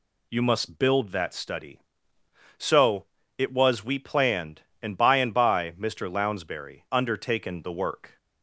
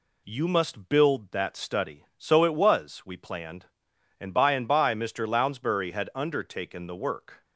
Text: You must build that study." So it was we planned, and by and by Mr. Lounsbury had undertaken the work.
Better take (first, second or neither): second